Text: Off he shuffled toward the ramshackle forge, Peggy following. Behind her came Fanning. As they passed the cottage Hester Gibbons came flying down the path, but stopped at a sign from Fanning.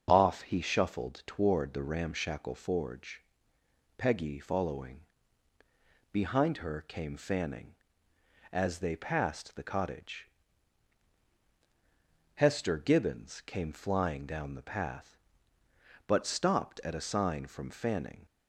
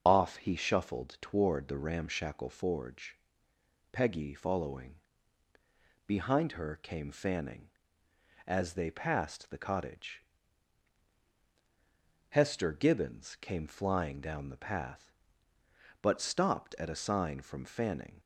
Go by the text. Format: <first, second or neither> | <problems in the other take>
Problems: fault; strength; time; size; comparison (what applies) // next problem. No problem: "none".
first | loses the start of "Off"; at 0.0 s; 30 ms // starts louder than the rest; until 1.0 s; 6.5 dB; also in the first // pauses between "cottage" and "Hester"; strong; at 10.2 s; 2.0 s long; strong in the first